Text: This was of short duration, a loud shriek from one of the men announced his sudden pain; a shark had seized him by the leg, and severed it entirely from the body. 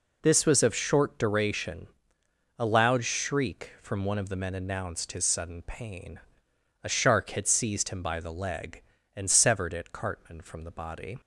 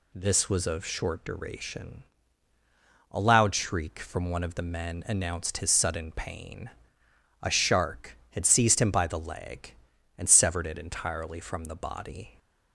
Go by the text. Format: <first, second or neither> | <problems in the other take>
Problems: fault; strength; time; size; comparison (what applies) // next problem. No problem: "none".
second | says "cartman" for "entirely"; at 9.9 s